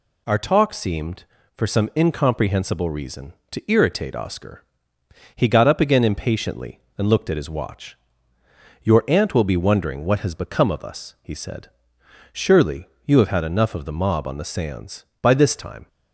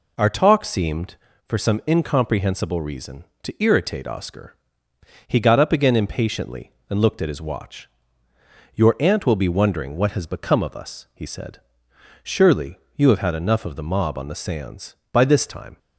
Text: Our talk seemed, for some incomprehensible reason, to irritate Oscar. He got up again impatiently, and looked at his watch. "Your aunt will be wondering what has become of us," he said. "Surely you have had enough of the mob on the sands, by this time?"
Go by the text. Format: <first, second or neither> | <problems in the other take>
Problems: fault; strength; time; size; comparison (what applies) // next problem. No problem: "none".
first | starts louder than the rest; until 1.4 s; 4 dB // pauses between "Surely" and "you"; slight; at 12.7 s; 0.20 s long; slight in the first